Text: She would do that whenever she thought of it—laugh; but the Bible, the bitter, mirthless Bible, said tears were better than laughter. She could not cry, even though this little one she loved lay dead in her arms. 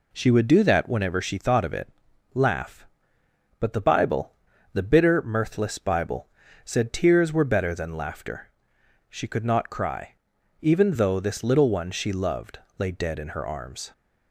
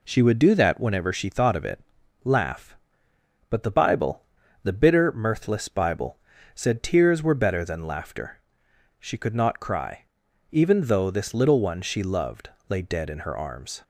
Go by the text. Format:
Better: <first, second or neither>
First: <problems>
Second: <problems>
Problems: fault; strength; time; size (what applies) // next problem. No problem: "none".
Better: neither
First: pauses between "loved" and "lay"; slight; at 12.5 s; 0.20 s long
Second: pauses between "loved" and "lay"; slight; at 12.4 s; 0.20 s long